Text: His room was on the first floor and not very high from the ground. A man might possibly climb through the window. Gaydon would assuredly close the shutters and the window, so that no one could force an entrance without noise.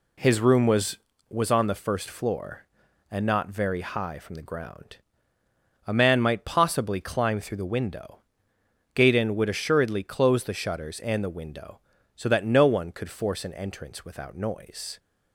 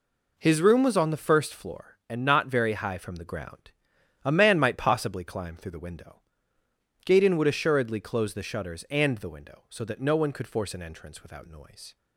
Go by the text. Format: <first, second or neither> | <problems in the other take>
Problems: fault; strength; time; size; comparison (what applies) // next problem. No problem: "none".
second | says "was" twice; at 1.2 s